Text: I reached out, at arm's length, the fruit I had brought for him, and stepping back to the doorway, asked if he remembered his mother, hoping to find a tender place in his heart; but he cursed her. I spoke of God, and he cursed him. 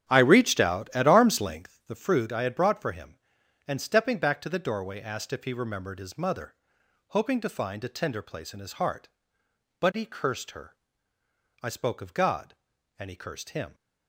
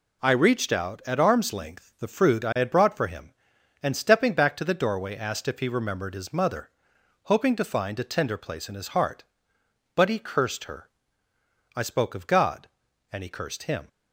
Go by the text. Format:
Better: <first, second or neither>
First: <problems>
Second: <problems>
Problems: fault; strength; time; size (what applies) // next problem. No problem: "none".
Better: second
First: starts louder than the rest; strong; until 1.8 s; 10 dB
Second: none